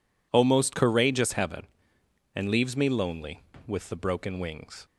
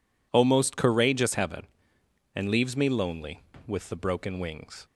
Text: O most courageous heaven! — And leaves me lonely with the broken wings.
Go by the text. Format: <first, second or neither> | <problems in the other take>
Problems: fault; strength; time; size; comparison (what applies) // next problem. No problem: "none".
neither | none